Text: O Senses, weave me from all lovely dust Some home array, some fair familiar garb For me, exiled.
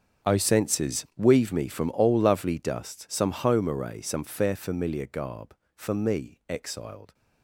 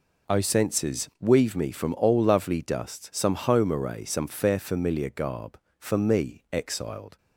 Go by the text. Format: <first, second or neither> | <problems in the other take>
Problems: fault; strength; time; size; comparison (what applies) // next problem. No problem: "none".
second | gets quieter; strong; throughout; 18 dB